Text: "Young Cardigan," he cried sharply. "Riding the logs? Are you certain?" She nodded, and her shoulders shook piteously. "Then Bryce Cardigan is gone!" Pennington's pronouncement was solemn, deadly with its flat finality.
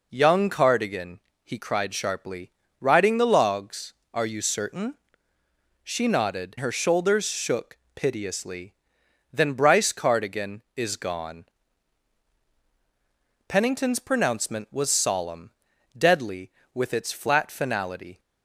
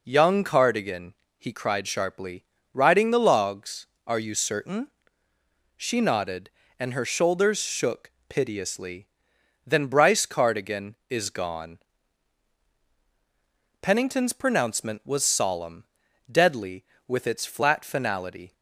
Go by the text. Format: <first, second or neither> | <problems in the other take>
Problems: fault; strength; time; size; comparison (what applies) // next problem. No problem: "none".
second | skips "and"; at 6.5 s // pauses between "shook" and "piteously"; slight; at 7.7 s; 0.18 s long; slight in the second